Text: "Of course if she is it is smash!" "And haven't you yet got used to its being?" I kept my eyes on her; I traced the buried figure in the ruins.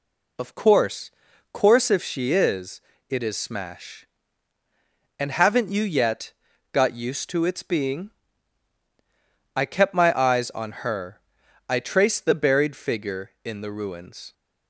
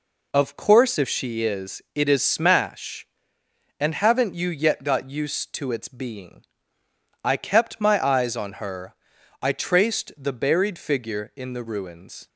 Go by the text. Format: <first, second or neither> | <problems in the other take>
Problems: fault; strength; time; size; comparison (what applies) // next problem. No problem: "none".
second | says "course" twice; at 1.5 s // pauses between "is" and "it"; slight; at 2.7 s; 0.28 s long // pauses between "yet" and "got"; at 6.3 s; 0.40 s long